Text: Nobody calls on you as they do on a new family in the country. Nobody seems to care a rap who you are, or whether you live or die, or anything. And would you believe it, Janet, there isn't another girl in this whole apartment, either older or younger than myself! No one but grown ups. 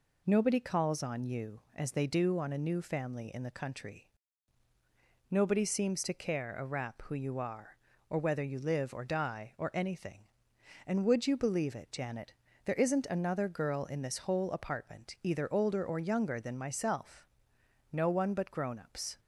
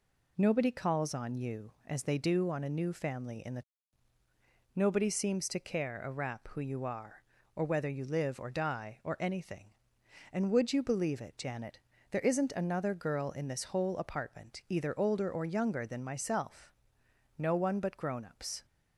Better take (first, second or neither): first